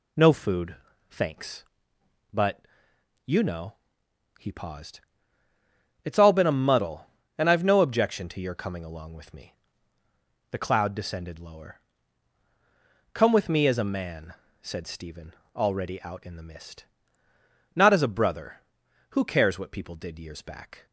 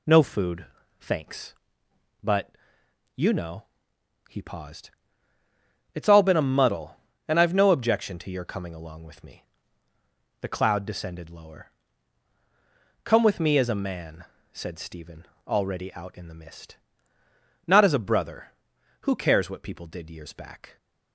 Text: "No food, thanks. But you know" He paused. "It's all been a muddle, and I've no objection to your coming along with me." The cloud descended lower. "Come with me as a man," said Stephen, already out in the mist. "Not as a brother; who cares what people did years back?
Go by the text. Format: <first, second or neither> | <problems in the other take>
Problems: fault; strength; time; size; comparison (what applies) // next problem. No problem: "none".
neither | pauses between "But" and "you"; noticeable; the same in both // pauses between "know" and "He"; noticeable; the same in both